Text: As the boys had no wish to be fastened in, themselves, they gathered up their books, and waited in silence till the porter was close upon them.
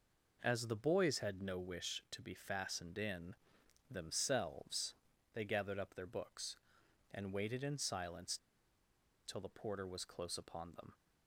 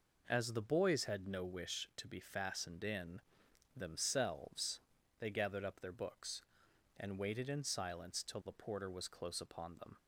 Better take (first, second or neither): second